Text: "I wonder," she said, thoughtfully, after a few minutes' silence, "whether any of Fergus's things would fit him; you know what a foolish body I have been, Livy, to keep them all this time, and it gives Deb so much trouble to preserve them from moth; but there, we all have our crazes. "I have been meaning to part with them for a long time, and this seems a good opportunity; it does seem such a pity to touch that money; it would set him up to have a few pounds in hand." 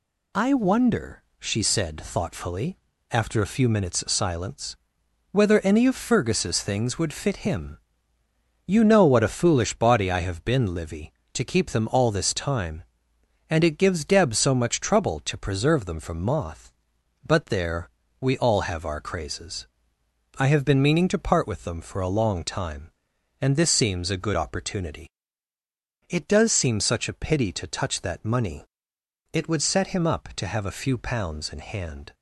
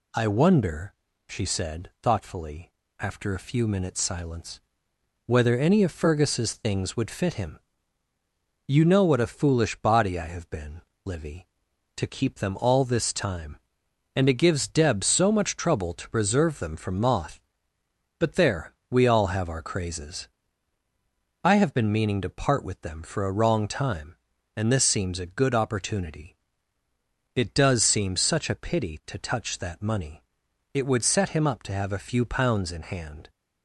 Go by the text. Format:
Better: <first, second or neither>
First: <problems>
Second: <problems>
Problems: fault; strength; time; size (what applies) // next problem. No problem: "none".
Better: first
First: none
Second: says "wrong" for "long"; at 23.3 s